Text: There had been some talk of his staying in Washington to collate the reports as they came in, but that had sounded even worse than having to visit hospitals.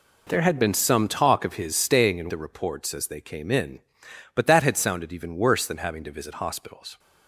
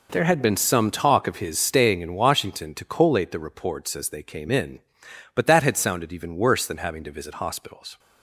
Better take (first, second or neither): second